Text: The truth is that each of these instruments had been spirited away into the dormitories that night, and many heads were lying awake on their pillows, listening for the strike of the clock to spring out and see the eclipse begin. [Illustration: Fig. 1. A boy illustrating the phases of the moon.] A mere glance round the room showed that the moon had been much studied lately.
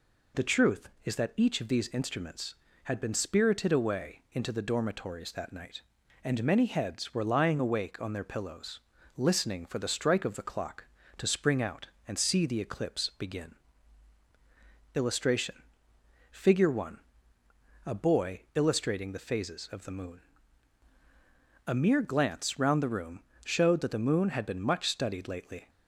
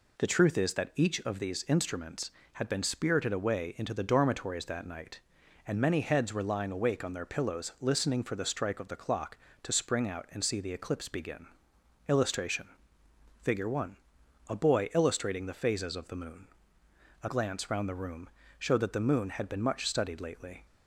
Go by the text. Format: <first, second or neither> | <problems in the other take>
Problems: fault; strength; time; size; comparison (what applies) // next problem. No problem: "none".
first | skips "mere"; at 17.2 s // pauses between "room" and "showed"; slight; at 18.2 s; 0.30 s long; slight in the first